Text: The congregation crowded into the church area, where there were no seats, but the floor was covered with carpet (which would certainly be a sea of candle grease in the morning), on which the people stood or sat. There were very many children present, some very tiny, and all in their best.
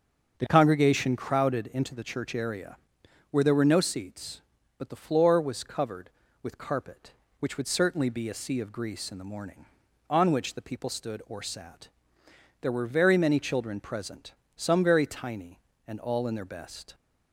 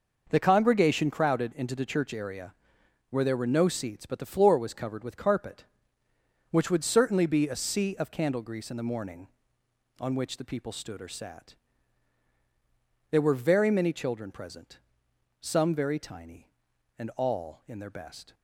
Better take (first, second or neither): second